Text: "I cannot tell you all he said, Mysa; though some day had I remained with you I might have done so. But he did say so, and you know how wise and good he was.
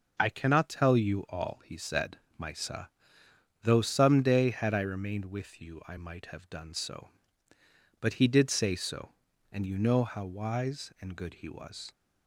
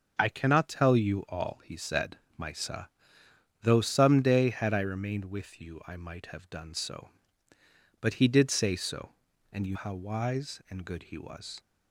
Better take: first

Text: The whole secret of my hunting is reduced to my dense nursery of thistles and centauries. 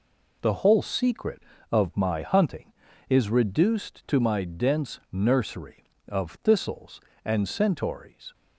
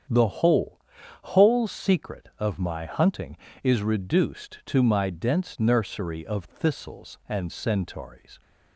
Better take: first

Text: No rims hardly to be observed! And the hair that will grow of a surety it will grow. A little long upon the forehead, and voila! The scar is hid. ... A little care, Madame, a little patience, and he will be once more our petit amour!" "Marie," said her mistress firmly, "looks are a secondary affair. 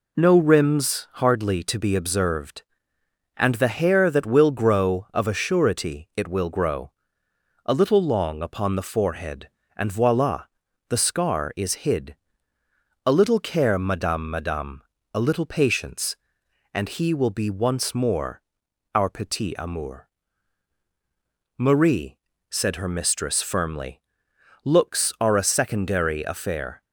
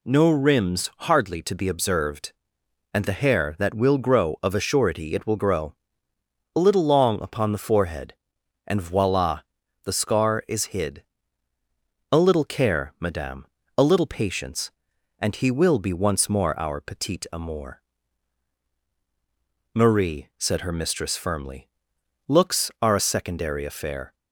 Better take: second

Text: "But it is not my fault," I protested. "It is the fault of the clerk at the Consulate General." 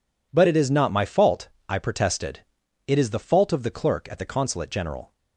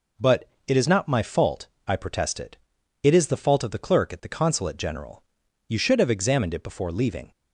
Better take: first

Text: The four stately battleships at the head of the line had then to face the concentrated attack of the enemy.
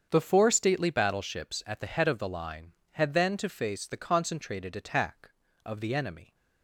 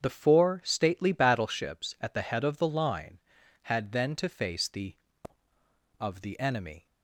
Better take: first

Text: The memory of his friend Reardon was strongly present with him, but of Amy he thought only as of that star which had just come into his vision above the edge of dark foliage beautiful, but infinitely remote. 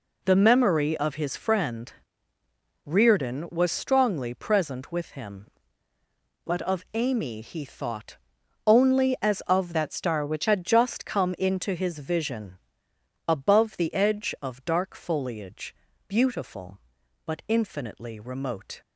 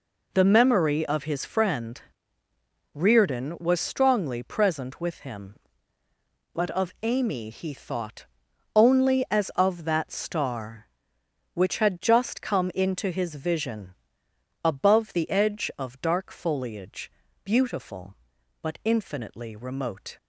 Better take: second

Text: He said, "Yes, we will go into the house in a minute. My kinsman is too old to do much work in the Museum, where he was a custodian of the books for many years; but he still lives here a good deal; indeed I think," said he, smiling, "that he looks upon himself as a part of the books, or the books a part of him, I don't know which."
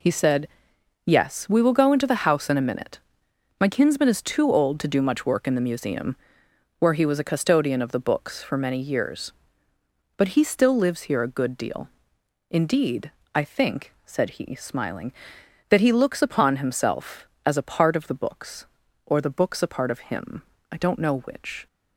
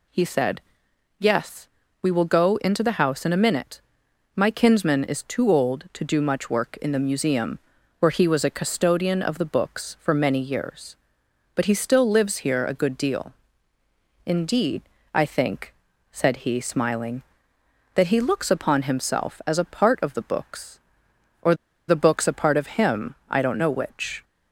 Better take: first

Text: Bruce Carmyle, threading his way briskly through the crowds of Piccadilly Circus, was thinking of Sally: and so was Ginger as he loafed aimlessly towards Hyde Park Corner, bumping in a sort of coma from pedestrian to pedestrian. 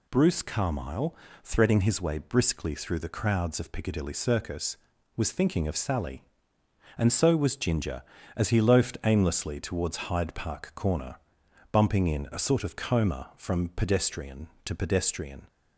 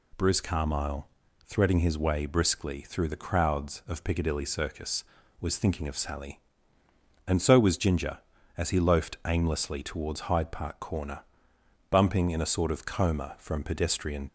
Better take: first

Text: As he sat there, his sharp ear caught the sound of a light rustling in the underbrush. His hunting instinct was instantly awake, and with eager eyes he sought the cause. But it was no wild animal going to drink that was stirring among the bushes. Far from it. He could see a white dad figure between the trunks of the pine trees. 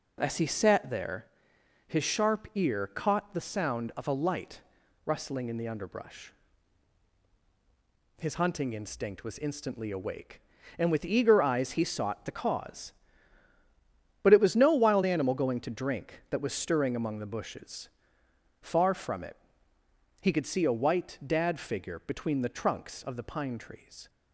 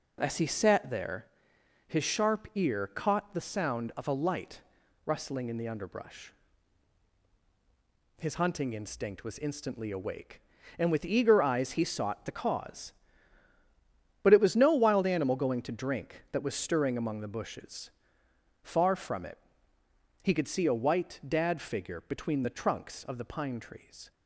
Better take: neither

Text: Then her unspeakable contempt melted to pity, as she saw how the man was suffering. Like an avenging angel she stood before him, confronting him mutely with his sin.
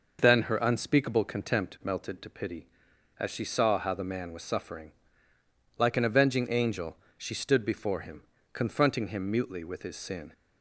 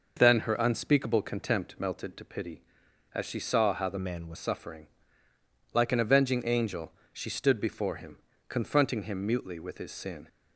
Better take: first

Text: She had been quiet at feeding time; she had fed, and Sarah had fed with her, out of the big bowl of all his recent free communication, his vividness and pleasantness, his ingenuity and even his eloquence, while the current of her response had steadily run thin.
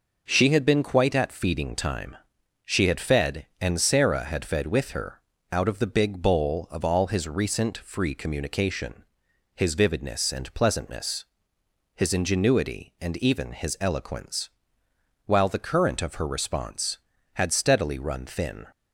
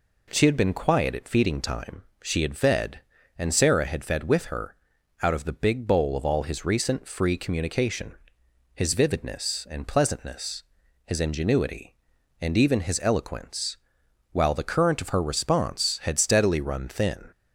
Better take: second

